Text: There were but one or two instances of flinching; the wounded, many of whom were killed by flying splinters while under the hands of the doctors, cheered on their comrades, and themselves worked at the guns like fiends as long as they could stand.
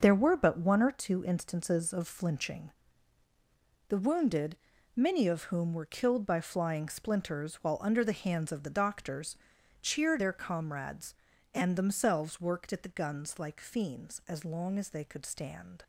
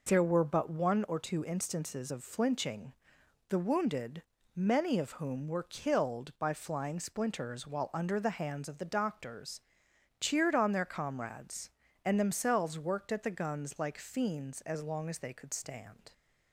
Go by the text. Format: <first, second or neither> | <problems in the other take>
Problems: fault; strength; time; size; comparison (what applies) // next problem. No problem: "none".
second | skips "on"; at 10.1 s